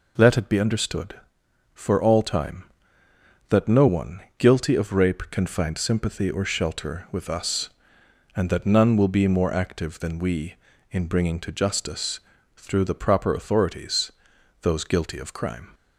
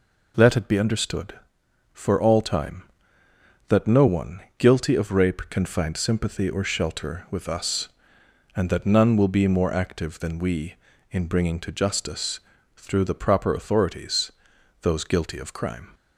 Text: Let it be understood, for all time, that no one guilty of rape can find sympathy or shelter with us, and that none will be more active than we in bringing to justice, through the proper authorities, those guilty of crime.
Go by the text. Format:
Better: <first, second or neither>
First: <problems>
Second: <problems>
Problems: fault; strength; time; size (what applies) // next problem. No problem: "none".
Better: neither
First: pauses between "one" and "guilty"; slight; at 4.2 s; 0.18 s long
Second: pauses between "one" and "guilty"; slight; at 4.4 s; 0.18 s long